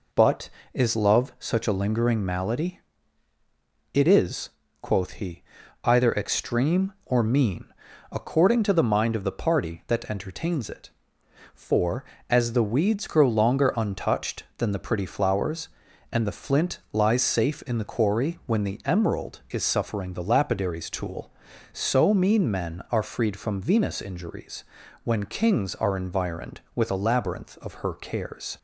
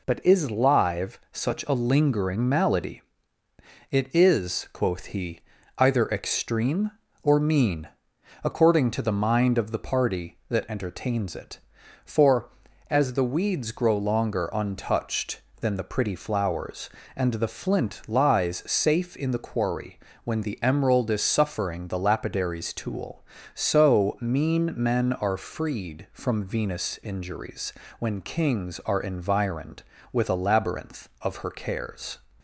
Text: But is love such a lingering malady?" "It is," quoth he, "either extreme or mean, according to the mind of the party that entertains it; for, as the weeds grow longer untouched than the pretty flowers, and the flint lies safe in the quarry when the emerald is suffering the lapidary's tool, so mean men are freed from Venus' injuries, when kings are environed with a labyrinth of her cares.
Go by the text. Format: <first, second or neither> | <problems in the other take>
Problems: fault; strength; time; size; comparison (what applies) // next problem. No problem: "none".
first | says "live" for "love"; at 0.4 s // pauses between "quarry" and "when"; slight; at 19.9 s; 0.24 s long